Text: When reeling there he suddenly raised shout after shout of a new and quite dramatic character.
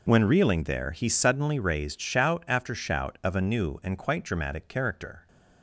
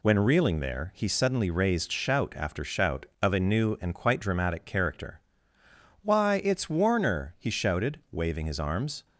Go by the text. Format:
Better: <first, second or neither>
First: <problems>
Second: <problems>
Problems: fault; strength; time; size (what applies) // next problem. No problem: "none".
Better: first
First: none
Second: goes on to say "Why it's Warner he shouted waving his arms"; strong; from 6.0 s on; 3.0 s long